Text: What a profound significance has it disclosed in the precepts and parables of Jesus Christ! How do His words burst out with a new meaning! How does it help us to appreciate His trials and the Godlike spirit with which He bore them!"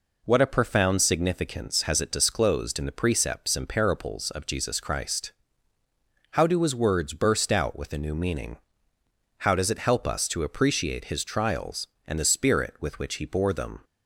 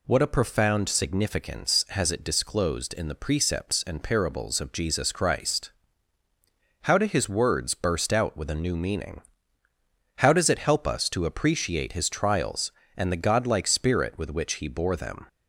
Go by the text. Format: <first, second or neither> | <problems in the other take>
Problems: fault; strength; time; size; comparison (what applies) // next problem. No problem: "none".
second | skips "Godlike"; at 12.2 s